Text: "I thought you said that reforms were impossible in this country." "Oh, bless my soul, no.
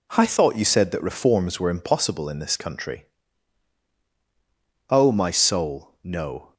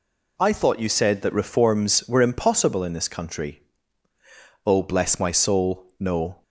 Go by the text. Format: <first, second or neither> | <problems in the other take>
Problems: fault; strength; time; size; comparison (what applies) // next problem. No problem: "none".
second | skips "bless"; at 5.1 s